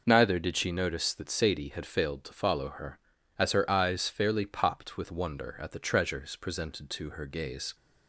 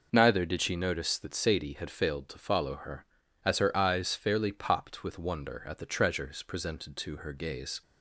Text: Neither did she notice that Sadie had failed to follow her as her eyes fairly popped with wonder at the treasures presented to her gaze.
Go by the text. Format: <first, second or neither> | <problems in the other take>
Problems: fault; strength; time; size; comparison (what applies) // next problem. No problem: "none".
neither | none